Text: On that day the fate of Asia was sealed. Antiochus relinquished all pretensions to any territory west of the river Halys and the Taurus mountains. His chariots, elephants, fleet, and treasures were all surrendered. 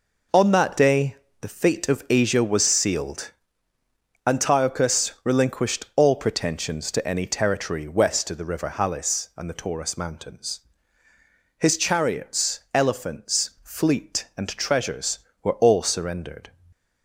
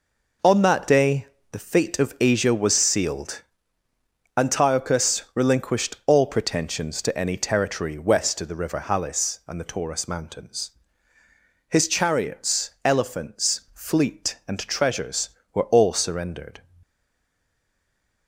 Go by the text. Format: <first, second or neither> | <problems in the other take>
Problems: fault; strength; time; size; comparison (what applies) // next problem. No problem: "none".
first | pauses between "day" and "the"; slight; at 1.2 s; 0.24 s long; slight in the first // stays silent after the last word; noticeable; from 16.8 s on; 1.4 s long